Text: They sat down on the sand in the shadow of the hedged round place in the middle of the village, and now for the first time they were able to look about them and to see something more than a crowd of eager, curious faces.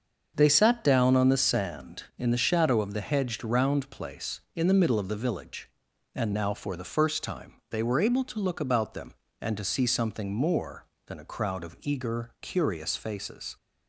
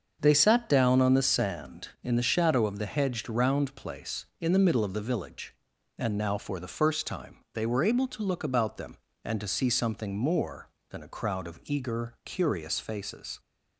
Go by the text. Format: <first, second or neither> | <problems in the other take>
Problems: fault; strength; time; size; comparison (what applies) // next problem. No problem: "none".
neither | starts louder than the rest; the same in both // pauses between "time" and "they"; slight; the same in both